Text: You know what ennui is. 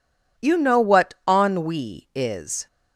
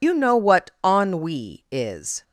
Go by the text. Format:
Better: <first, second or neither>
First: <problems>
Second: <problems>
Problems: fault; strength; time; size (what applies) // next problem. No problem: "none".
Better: first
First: none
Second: loses the start of "You"; at 0.0 s; 70 ms